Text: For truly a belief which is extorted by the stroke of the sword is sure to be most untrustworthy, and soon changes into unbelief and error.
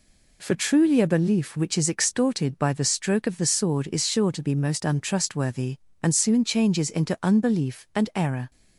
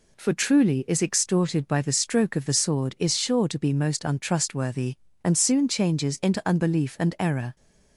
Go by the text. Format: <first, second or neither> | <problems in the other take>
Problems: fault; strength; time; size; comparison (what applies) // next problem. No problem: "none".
first | skips "a belief which"; at 0.8 s